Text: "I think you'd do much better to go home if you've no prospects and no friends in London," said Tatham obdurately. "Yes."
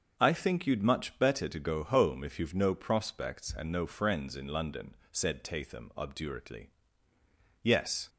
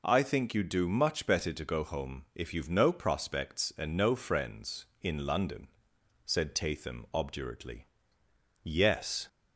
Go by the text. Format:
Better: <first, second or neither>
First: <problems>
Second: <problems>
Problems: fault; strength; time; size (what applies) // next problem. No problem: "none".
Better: second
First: starts louder than the rest; until 1.1 s; 6 dB // skips "do"; at 0.8 s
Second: none